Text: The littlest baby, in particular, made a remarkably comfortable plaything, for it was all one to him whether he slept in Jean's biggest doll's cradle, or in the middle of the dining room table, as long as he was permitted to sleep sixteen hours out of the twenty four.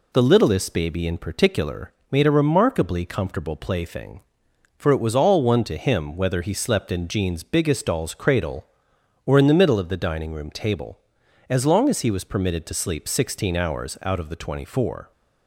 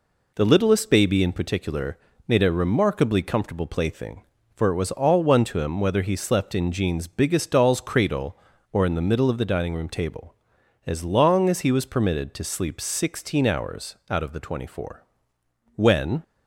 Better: first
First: none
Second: pauses between "hours" and "out"; slight; at 13.9 s; 0.16 s long // goes on to say "When"; slight; from 15.7 s on; 0.46 s long

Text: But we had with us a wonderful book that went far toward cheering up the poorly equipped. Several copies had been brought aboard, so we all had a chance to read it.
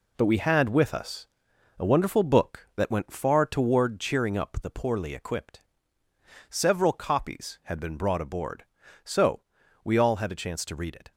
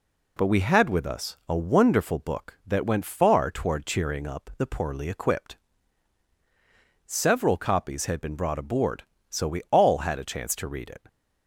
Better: second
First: gets quieter; throughout; 7 dB // pauses between "us" and "a"; noticeable; at 1.2 s; 0.52 s long // pauses between "so" and "we"; at 9.4 s; 0.42 s long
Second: none

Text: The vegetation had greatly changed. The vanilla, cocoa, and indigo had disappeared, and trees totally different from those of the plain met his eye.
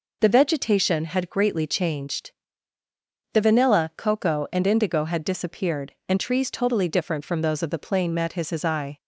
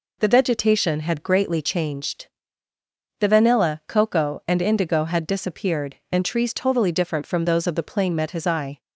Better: second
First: says "his" twice; at 8.4 s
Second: none

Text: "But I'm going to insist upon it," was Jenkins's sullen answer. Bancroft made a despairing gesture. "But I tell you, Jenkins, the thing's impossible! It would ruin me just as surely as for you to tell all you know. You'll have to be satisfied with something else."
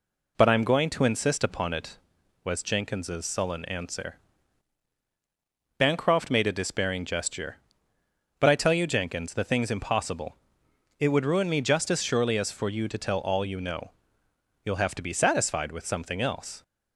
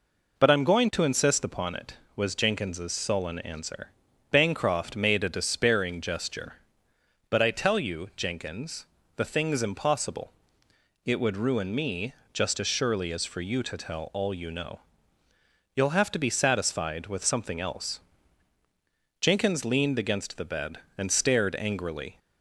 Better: first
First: none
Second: pauses between "me" and "just"; slight; at 12.1 s; 0.18 s long // goes on to say "Jenkins leaned against the bed and stared angrily"; strong; from 19.2 s on; 2.9 s long

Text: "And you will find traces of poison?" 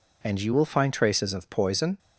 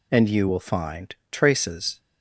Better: first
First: none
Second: pauses between "find" and "traces"; slight; at 1.1 s; 0.16 s long // stops before "of poison"; at 2.0 s

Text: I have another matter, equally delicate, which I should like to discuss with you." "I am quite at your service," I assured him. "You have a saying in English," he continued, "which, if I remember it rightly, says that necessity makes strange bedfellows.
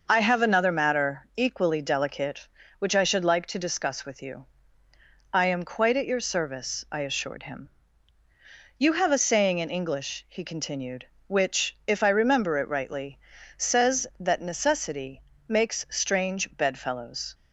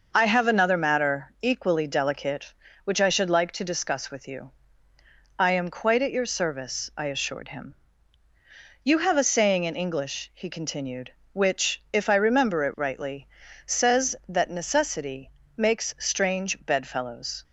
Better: neither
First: pauses between "necessity" and "makes"; slight; at 15.2 s; 0.26 s long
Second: pauses between "necessity" and "makes"; slight; at 15.3 s; 0.26 s long

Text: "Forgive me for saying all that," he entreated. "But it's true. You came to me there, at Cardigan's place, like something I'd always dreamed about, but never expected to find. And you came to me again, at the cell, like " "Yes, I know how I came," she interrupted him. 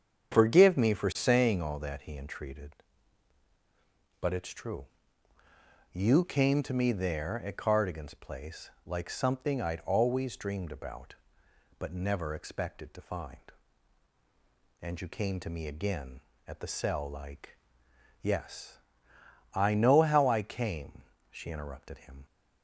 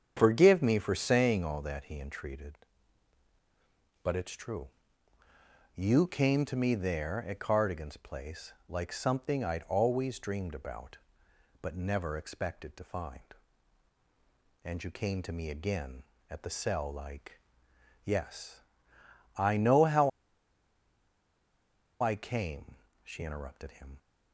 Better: first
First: starts louder than the rest; strong; until 1.3 s; 7.5 dB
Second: starts louder than the rest; strong; until 1.1 s; 7.5 dB // pauses between "how" and "I"; strong; at 20.0 s; 1.9 s long

